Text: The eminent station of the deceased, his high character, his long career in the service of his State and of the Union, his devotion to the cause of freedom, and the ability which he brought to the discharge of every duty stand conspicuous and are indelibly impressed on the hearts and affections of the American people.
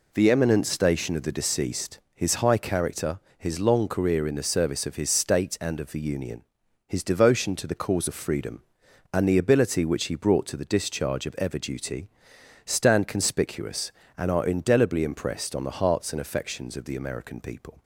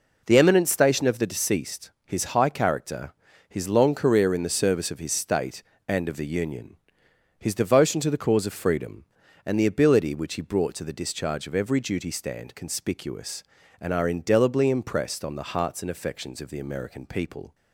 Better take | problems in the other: second | says "ever" for "every"; at 11.3 s // pauses between "duty" and "stand"; noticeable; at 12.0 s; 0.56 s long

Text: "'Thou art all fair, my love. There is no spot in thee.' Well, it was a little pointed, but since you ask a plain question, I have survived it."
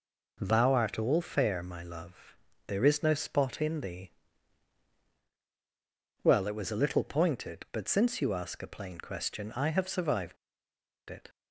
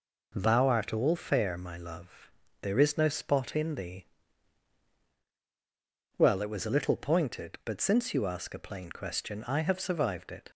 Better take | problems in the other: second | pauses between "survived" and "it"; noticeable; at 10.3 s; 0.72 s long

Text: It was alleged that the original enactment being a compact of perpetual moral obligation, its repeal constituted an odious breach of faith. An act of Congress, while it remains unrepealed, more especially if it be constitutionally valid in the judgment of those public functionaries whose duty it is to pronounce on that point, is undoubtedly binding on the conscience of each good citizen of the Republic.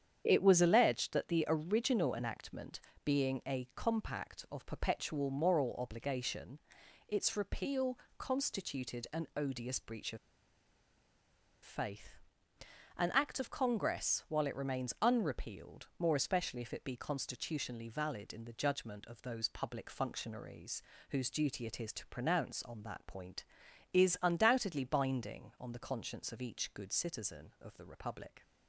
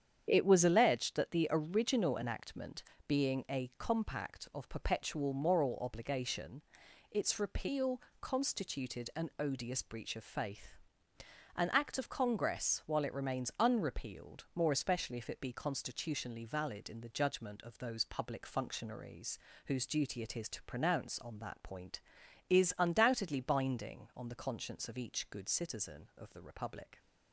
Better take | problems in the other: second | starts louder than the rest; strong; until 1.2 s; 8.5 dB; strong in the second // pauses between "enactment" and "being"; slight; at 2.8 s; 0.24 s long; slight in the second // pauses between "repeal" and "constituted"; slight; at 7.9 s; 0.22 s long; slight in the second // pauses between "of" and "faith"; strong; at 10.1 s; 1.4 s long // pauses between "functionaries" and "whose"; slight; at 20.8 s; 0.28 s long; slight in the second

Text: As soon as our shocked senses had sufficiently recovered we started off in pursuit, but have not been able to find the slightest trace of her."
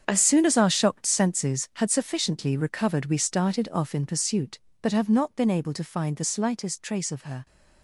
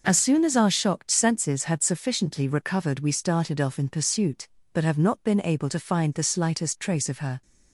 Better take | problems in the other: second | gets quieter; strong; throughout; 12 dB

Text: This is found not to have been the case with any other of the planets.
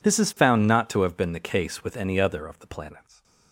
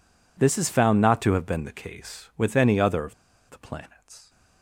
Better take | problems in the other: first | pauses between "of" and "the"; slight; at 3.1 s; 0.35 s long

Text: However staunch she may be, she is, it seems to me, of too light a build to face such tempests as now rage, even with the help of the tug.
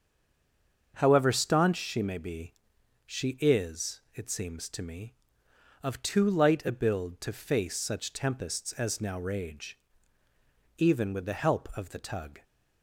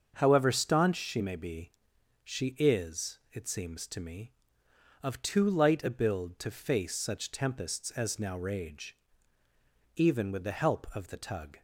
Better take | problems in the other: second | stays silent before the first word; slight; until 0.9 s; 0.9 s long // starts louder than the rest; until 1.9 s; 7 dB; also in the second

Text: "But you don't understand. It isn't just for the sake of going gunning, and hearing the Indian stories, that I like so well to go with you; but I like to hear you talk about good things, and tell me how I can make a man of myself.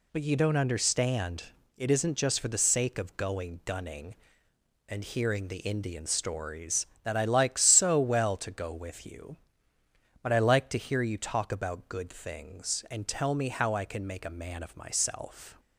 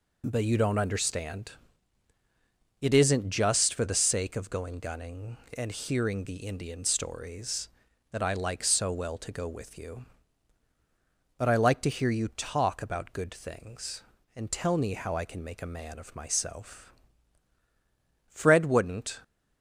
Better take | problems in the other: first | goes on to say "Fred wouldn't"; noticeable; from 18.3 s on; 0.90 s long

